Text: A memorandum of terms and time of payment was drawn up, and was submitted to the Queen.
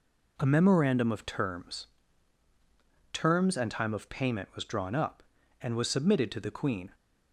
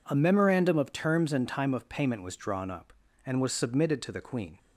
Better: second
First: says "terms" twice; at 3.1 s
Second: none

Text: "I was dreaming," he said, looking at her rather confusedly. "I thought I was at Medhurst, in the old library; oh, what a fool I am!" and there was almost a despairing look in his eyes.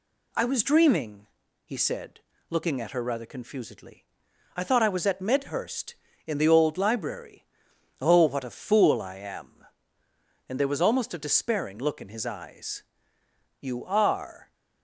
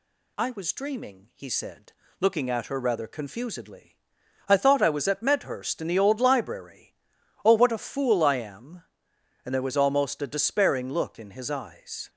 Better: second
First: goes on to say "You are"; noticeable; from 13.5 s on; 0.94 s long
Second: none

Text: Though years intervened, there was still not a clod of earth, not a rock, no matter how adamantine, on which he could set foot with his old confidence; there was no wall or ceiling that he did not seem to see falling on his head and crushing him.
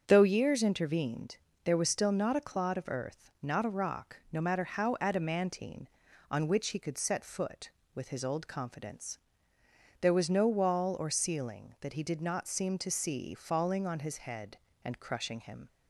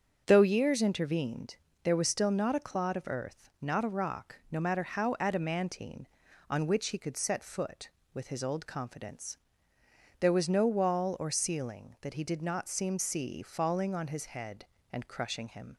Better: first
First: starts louder than the rest; until 1.0 s; 6.5 dB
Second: starts louder than the rest; until 1.2 s; 6.5 dB // skips "to"; at 12.9 s

